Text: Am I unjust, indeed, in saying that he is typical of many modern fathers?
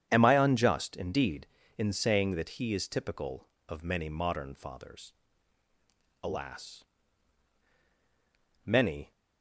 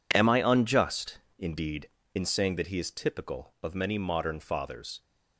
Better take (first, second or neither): second